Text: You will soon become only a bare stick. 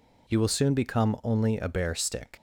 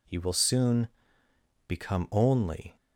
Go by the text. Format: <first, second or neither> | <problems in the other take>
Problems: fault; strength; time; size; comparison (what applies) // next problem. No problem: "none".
first | pauses between "soon" and "become"; noticeable; at 0.8 s; 0.78 s long // stops before "a bare stick"; at 2.7 s